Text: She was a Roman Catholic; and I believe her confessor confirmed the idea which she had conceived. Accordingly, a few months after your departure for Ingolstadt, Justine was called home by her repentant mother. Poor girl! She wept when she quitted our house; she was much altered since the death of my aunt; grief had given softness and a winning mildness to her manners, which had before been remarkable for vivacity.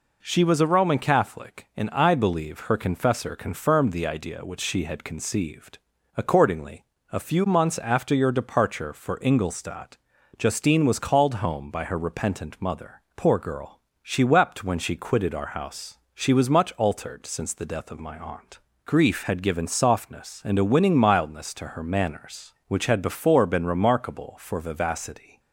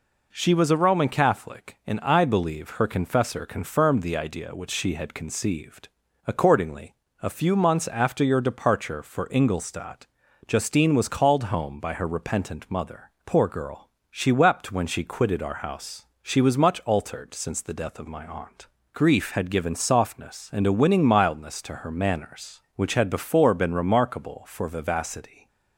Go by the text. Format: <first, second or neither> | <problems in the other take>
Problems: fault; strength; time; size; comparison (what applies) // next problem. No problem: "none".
neither | none